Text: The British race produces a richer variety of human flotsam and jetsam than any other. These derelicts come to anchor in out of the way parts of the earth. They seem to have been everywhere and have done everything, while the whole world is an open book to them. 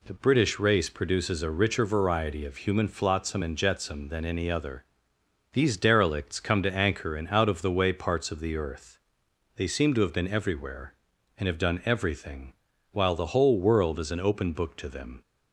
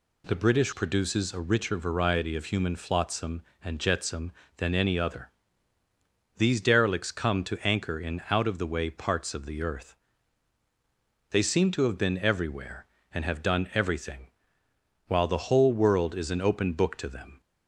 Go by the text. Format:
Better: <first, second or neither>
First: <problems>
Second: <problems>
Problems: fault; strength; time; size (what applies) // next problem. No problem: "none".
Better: first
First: none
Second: skips "race"; at 0.7 s